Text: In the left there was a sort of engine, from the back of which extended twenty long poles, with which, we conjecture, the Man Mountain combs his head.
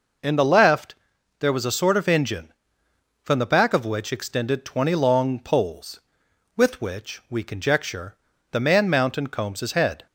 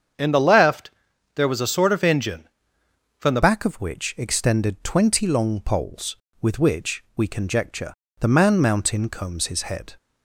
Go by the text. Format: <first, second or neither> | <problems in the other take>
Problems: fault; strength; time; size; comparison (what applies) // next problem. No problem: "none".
first | starts louder than the rest; strong; until 1.6 s; 7.5 dB // pauses between "left" and "there"; at 0.9 s; 0.44 s long; also in the first // changes voice at "back"; from 3.4 s on; 6.5 s long